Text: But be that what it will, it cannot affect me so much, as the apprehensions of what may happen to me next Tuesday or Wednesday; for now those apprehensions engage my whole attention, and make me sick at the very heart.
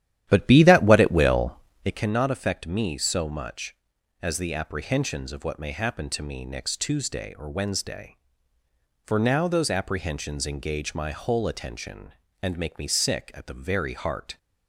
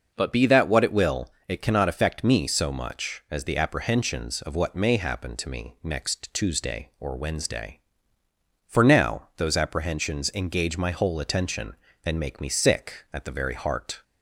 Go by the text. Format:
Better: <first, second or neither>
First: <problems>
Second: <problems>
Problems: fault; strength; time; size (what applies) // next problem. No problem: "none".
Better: second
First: starts louder than the rest; strong; until 2.1 s; 11.5 dB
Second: none